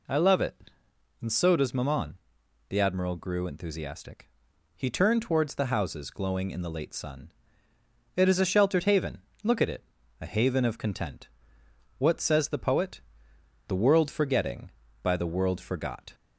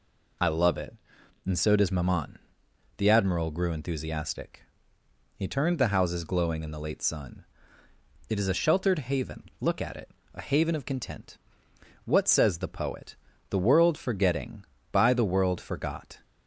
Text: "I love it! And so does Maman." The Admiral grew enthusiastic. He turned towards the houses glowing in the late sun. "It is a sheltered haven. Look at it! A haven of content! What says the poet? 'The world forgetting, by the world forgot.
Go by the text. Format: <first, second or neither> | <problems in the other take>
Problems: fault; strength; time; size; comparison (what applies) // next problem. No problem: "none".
first | skips "towards"; at 5.7 s